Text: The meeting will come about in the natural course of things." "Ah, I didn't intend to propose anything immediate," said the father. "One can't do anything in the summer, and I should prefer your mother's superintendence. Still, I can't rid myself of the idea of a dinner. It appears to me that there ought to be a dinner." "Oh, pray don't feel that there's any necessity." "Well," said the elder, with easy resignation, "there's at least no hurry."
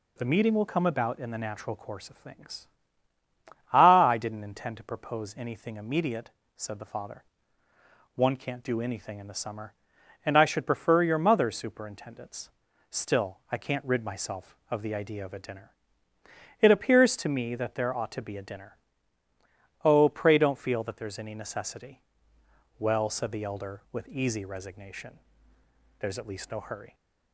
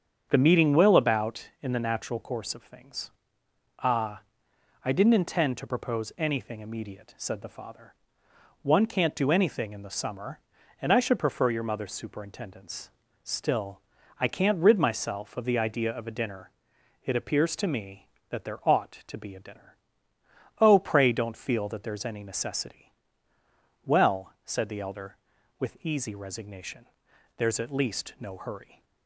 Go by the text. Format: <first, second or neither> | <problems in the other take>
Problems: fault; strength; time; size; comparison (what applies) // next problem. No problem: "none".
first | starts louder than the rest; strong; until 1.3 s; 7.5 dB // skips "come"; at 0.9 s